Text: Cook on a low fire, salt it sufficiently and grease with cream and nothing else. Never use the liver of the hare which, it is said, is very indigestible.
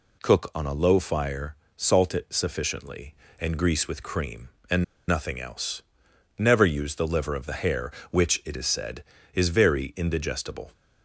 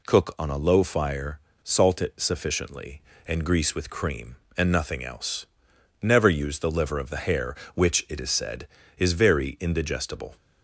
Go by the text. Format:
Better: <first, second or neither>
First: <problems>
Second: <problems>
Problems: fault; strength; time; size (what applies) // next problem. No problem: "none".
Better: second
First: pauses between "and" and "nothing"; slight; at 4.8 s; 0.25 s long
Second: none